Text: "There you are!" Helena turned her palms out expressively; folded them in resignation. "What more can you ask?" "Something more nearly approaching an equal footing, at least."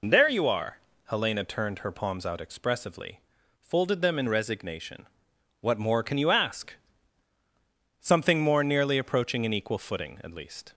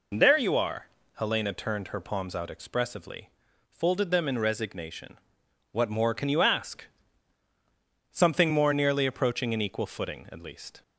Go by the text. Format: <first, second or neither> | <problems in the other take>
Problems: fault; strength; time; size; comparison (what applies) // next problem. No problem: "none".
neither | none